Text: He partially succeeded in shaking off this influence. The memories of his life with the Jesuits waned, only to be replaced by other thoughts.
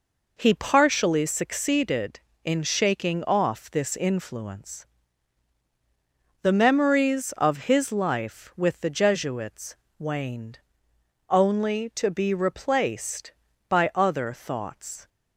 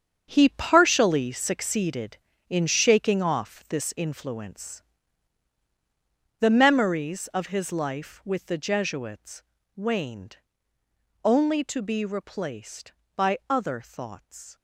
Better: first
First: pauses between "Jesuits" and "waned"; slight; at 9.7 s; 0.22 s long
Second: gets quieter; strong; throughout; 10.5 dB // pauses between "Jesuits" and "waned"; slight; at 9.4 s; 0.32 s long

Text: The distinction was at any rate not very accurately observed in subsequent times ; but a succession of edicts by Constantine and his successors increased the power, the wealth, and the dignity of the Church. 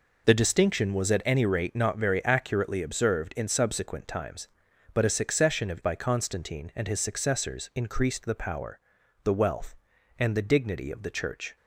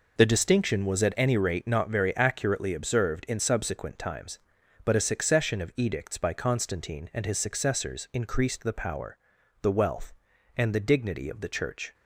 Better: second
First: skips "edicts"; at 5.8 s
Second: none

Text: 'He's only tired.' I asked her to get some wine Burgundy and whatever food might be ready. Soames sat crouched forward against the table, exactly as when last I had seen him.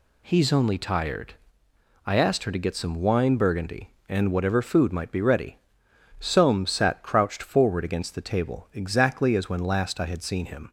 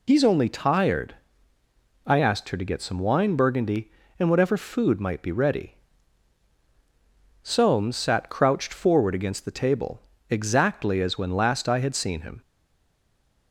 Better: first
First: none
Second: stays silent after the last word; from 12.4 s on; 1.1 s long

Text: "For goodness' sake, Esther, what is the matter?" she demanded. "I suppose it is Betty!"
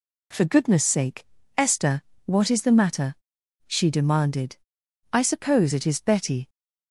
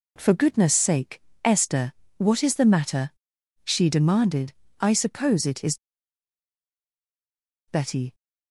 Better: first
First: none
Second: pauses between "is" and "Betty"; strong; at 5.7 s; 1.9 s long

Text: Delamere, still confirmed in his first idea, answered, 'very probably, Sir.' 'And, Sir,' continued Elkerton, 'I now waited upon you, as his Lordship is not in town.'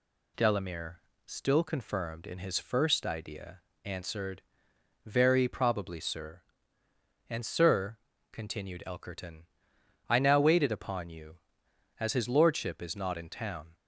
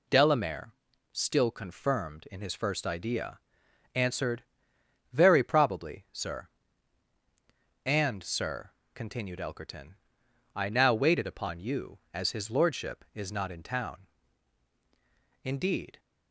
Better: first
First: none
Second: goes on to say "Indeed"; from 15.4 s on; 0.56 s long

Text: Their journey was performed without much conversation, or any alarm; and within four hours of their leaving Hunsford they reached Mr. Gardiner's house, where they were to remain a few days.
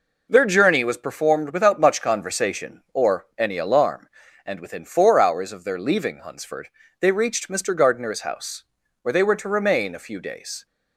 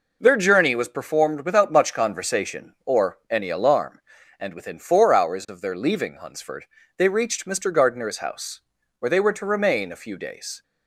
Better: neither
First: pauses between "Hunsford" and "they"; slight; at 6.6 s; 0.30 s long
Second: pauses between "Hunsford" and "they"; slight; at 6.6 s; 0.30 s long

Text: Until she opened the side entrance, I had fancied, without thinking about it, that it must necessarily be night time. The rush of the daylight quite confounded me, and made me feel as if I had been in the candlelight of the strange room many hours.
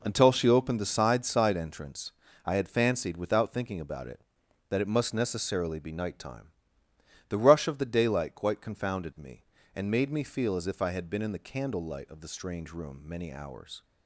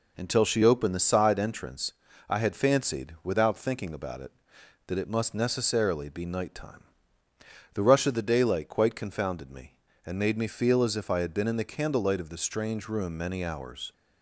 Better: second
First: says "side" twice; at 1.2 s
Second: none

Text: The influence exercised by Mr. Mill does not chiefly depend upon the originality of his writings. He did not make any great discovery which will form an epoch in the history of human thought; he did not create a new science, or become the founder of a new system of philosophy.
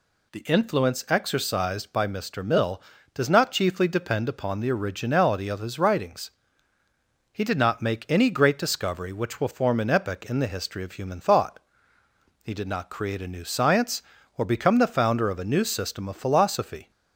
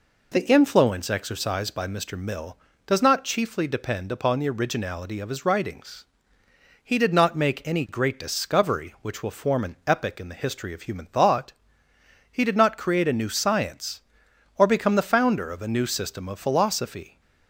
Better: neither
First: none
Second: none

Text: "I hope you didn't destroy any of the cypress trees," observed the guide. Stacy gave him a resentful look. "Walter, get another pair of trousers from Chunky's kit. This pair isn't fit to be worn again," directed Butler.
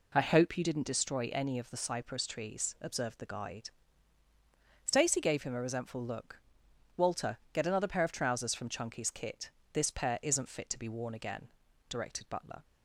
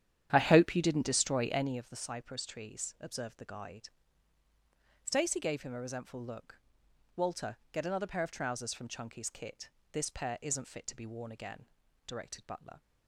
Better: first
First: none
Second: starts louder than the rest; strong; until 1.9 s; 10 dB

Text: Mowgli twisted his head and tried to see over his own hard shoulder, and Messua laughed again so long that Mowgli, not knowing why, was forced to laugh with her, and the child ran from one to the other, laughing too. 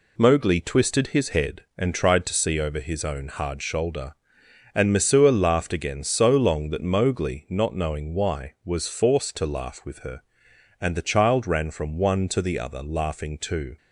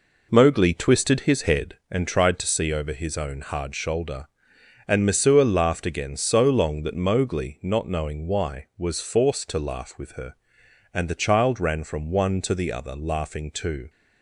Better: first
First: none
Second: starts louder than the rest; noticeable; until 1.9 s; 4.5 dB

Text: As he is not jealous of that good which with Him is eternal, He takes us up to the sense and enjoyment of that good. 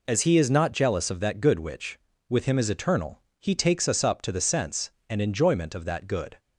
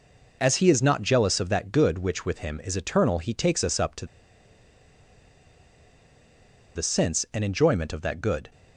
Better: first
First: none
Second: pauses between "to" and "the"; strong; at 4.0 s; 2.6 s long

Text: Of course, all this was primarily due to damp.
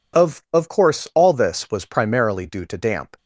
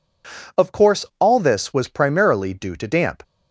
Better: second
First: says "Of" twice; at 0.5 s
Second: none

